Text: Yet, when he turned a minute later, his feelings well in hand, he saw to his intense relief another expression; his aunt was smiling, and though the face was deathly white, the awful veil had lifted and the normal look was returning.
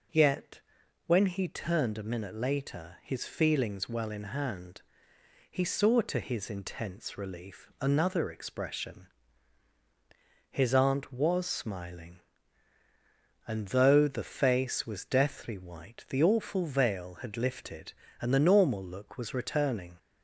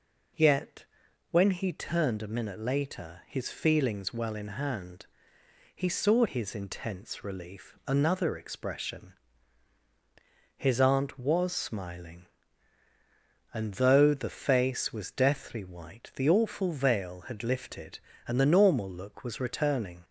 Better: first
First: none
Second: skips "to"; at 6.2 s

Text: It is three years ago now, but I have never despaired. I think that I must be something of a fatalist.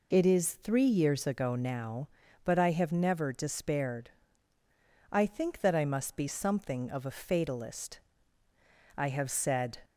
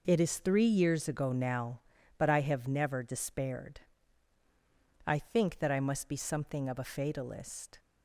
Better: second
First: goes on to say "I have said"; noticeable; from 8.9 s on; 0.80 s long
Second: none

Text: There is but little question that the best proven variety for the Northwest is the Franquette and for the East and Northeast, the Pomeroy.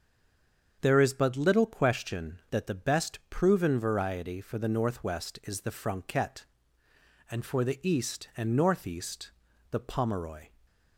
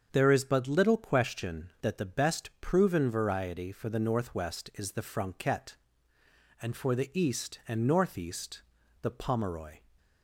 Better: second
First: stays silent before the first word; slight; until 0.8 s; 0.8 s long // starts louder than the rest; until 1.8 s; 7 dB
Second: starts louder than the rest; until 1.1 s; 7 dB

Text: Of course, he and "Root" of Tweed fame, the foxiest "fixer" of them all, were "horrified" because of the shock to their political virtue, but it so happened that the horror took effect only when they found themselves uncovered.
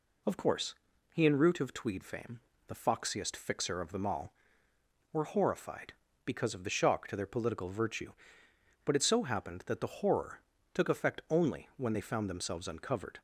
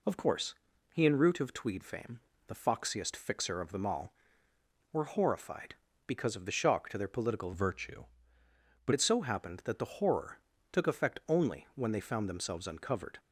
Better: first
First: pauses between "horror" and "took"; slight; at 10.3 s; 0.36 s long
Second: changes voice from "virtue" to "but"; from 7.5 to 8.9 s; 1.4 s long // pauses between "horror" and "took"; slight; at 10.3 s; 0.36 s long

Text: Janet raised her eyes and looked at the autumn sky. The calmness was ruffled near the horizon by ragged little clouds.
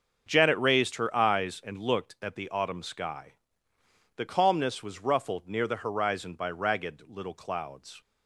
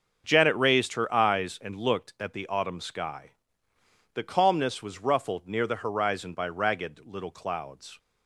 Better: neither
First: starts louder than the rest; until 1.2 s; 6.5 dB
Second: starts louder than the rest; until 1.2 s; 6.5 dB

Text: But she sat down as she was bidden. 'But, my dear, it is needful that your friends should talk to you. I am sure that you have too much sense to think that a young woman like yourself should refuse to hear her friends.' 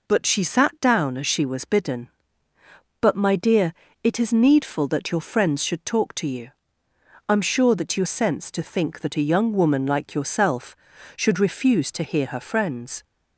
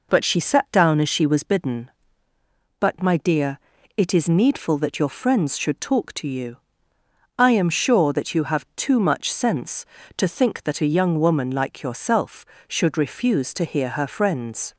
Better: second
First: skips "have too much"; at 8.0 s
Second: none

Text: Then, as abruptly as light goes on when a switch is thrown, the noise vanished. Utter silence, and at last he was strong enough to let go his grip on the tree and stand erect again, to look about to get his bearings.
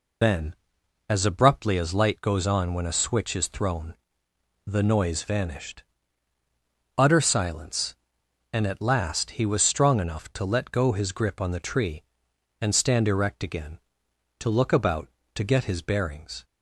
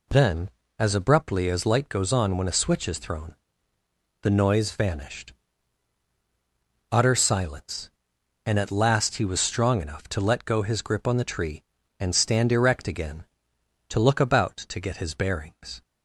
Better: second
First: loses the start of "Then"; at 0.2 s; 95 ms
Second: none

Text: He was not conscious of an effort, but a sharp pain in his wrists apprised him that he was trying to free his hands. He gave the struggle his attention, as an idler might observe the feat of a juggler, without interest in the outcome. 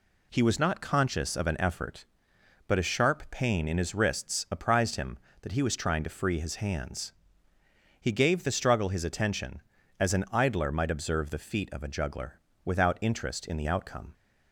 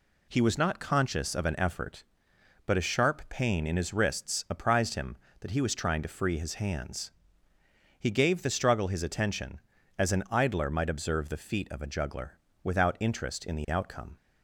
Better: neither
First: none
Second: none

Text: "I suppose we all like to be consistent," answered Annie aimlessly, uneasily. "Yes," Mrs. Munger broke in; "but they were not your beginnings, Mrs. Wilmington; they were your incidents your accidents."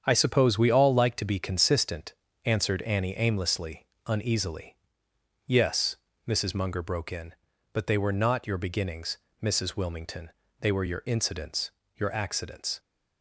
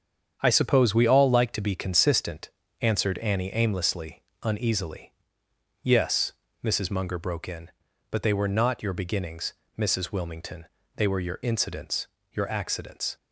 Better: neither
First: starts louder than the rest; strong; until 1.0 s; 8 dB // pauses between "incidents" and "your"; slight; at 11.7 s; 0.26 s long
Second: starts louder than the rest; strong; until 1.4 s; 8 dB // pauses between "incidents" and "your"; slight; at 12.0 s; 0.26 s long

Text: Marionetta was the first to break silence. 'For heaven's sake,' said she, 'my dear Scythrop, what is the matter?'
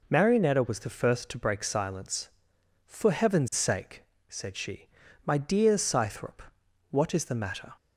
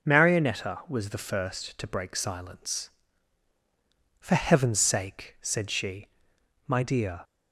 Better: first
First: none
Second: stops before "Scythrop what is the matter"; at 7.2 s

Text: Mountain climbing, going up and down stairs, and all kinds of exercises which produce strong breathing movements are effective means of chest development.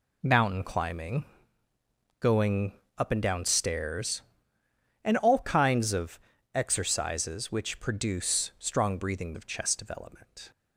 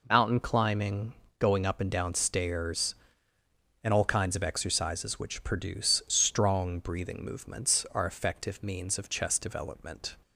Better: second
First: pauses between "going" and "up"; slight; at 2.7 s; 0.24 s long // pauses between "of" and "exercises"; slight; at 6.1 s; 0.34 s long // skips "movements are effective means"; at 9.3 s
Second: none

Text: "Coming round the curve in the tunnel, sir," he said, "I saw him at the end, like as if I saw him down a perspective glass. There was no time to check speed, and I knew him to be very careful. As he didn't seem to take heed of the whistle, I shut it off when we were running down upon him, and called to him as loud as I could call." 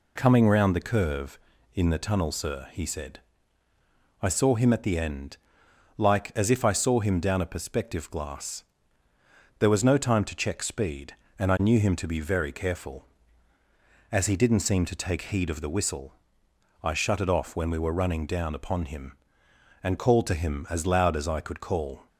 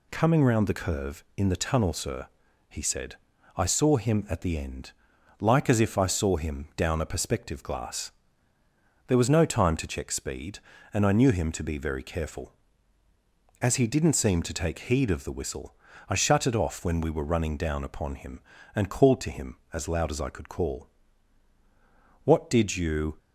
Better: first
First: none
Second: goes on to say "What did you"; noticeable; from 22.2 s on; 0.92 s long

